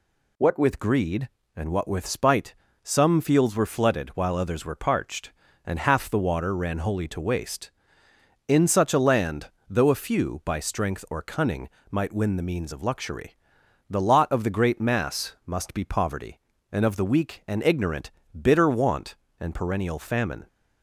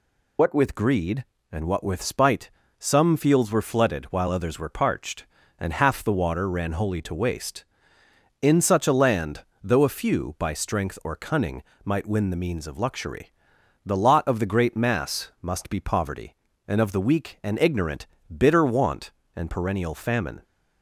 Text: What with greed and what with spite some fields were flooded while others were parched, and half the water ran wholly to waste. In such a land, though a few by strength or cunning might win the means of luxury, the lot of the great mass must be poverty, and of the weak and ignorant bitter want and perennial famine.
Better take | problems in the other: first | loses the start of "What"; at 0.3 s; 65 ms // pauses between "spite" and "some"; slight; at 2.5 s; 0.28 s long; slight in the first // pauses between "cunning" and "might"; slight; at 11.6 s; 0.22 s long; slight in the first // pauses between "ignorant" and "bitter"; slight; at 18.0 s; 0.28 s long; slight in the first

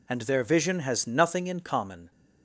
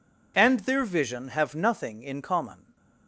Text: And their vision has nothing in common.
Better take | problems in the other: first | says "have" for "has"; at 1.2 s

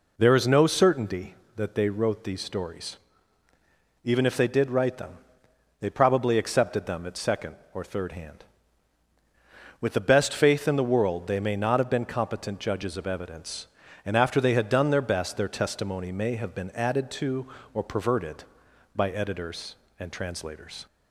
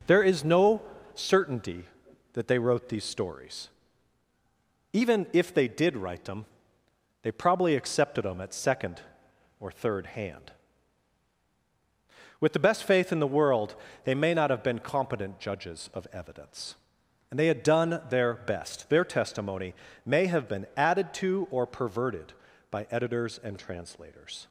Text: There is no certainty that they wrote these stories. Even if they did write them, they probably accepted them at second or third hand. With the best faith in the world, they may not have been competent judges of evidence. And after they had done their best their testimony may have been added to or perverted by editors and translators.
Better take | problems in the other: first | pauses between "no" and "certainty"; slight; at 0.8 s; 0.32 s long // skips "after"; at 17.3 s // pauses between "testimony" and "may"; slight; at 19.7 s; 0.32 s long

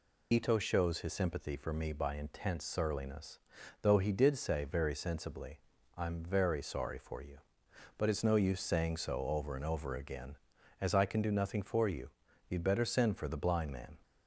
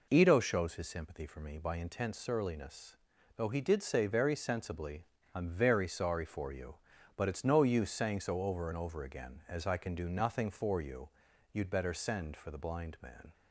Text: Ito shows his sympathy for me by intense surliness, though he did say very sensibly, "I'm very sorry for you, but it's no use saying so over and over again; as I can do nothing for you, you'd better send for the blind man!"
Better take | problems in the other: second | loses the start of "Ito"; at 0.3 s; 55 ms

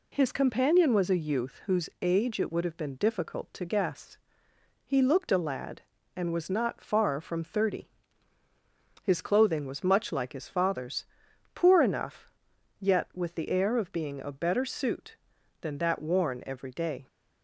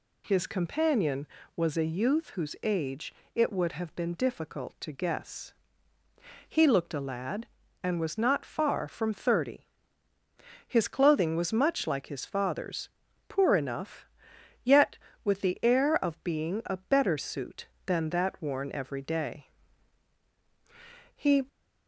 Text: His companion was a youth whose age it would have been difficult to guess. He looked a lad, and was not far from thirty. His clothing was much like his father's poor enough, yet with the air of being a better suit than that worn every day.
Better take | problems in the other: first | pauses between "age" and "it"; slight; at 3.1 s; 0.22 s long // pauses between "father's" and "poor"; at 12.8 s; 0.40 s long; noticeable in the first // goes on to say "He"; slight; from 21.1 s on; 0.30 s long

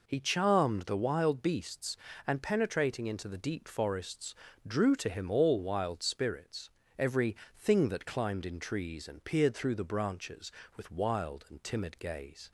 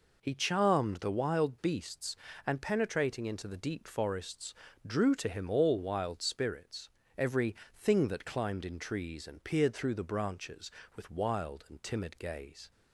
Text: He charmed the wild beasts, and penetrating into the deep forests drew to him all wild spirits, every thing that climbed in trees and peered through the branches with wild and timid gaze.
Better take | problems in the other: neither | pauses between "forests" and "drew"; slight; the same in both // pauses between "every" and "thing"; slight; the same in both

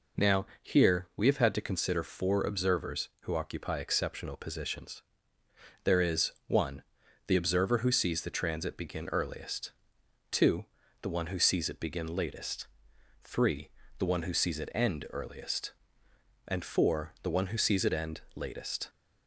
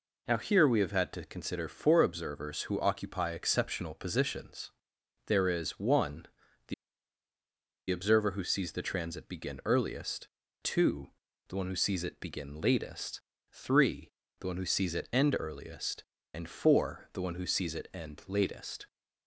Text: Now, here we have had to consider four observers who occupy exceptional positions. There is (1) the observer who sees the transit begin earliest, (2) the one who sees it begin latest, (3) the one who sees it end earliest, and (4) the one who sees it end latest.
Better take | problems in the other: first | pauses between "the" and "observer"; at 6.7 s; 1.1 s long

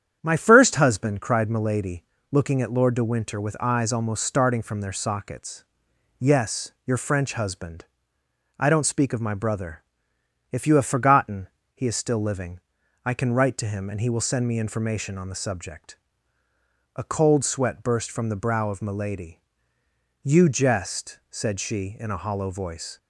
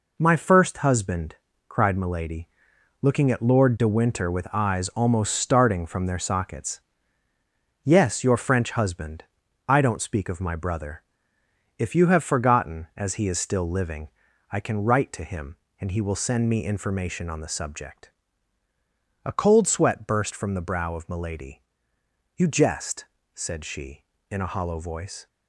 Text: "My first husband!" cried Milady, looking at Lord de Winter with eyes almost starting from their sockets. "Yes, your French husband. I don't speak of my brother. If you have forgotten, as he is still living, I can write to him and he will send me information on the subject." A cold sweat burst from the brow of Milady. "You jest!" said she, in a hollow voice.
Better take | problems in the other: second | starts louder than the rest; strong; until 1.2 s; 9 dB // skips "as"; at 11.6 s

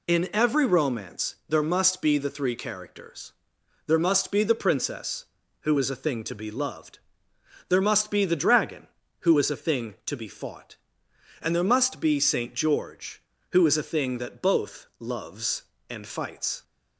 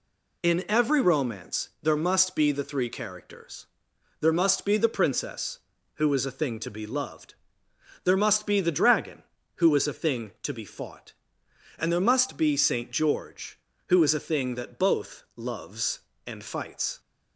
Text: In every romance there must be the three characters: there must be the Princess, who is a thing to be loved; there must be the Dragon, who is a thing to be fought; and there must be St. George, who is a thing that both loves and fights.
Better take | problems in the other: neither | none

